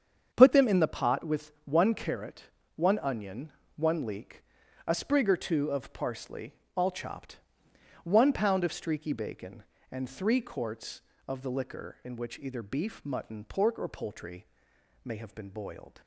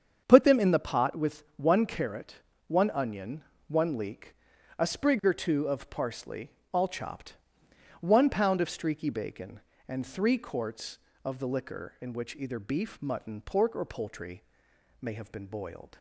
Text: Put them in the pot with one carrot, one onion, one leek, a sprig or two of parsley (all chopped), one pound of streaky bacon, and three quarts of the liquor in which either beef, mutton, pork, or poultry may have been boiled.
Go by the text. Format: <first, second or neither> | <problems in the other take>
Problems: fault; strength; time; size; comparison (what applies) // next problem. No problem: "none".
neither | starts louder than the rest; strong; the same in both // pauses between "poultry" and "may"; noticeable; the same in both